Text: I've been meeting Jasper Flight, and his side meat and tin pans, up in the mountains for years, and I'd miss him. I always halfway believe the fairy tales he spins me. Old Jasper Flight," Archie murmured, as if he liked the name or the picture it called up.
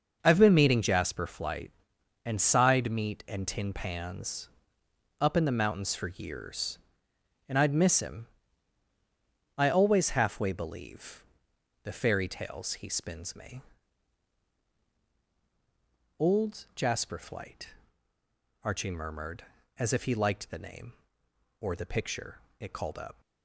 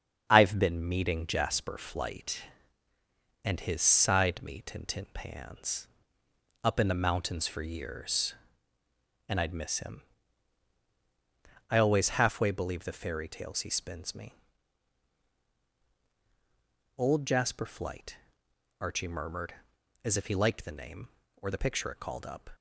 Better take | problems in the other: second | starts louder than the rest; noticeable; until 1.2 s; 6 dB; strong in the second // skips "his"; at 2.3 s // pauses between "believe" and "the"; noticeable; at 11.2 s; 0.60 s long // pauses between "picture" and "it"; slight; at 22.3 s; 0.18 s long

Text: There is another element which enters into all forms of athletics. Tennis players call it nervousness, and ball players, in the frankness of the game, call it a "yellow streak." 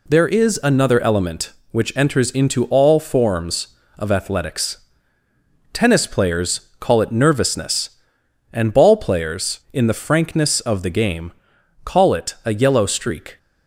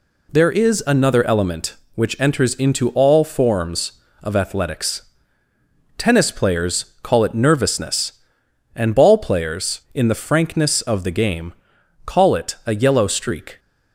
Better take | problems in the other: neither | none

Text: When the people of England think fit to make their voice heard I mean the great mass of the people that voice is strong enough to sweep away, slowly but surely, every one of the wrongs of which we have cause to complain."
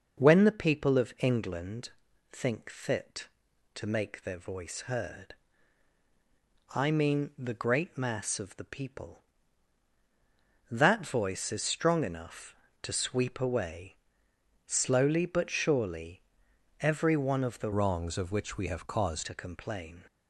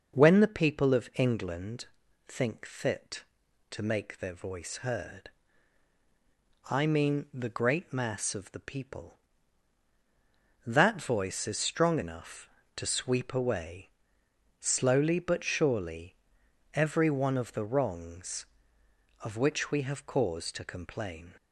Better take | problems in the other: second | pauses between "England" and "think"; at 1.9 s; 0.42 s long; also in the second // pauses between "heard" and "I"; strong; at 5.3 s; 1.4 s long; strong in the second // changes voice from "wrongs" to "cause"; from 17.7 to 19.2 s; 1.5 s long

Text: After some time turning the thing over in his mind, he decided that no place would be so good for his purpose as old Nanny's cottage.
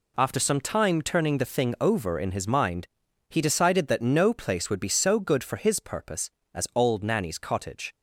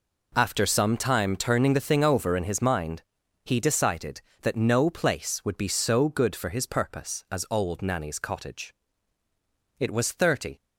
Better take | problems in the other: first | goes on to say "It was thirty"; noticeable; from 9.7 s on; 0.84 s long

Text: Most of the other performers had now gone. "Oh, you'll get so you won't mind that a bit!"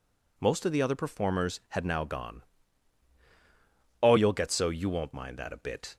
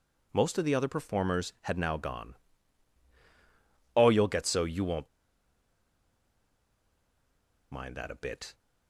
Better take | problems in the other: first | pauses between "won't" and "mind"; strong; at 5.0 s; 2.6 s long

